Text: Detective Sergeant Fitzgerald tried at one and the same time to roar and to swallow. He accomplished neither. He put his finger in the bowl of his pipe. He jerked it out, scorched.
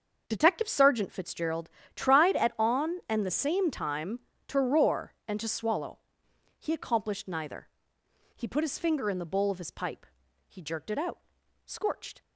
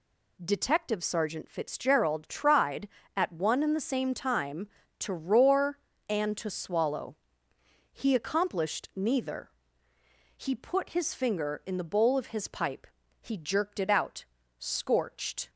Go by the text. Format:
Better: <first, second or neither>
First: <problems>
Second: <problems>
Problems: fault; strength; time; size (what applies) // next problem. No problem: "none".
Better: second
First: starts louder than the rest; until 1.2 s; 6.5 dB // pauses between "Fitzgerald" and "tried"; slight; at 1.6 s; 0.26 s long // says "on" for "one"; at 2.5 s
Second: none